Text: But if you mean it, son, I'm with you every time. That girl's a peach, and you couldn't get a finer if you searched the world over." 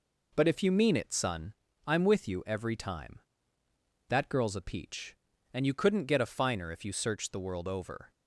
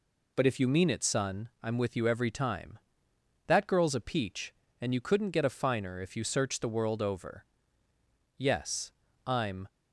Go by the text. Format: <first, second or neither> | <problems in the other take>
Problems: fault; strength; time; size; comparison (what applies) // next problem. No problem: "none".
first | goes on to say "Yes I'm"; noticeable; from 8.3 s on; 1.2 s long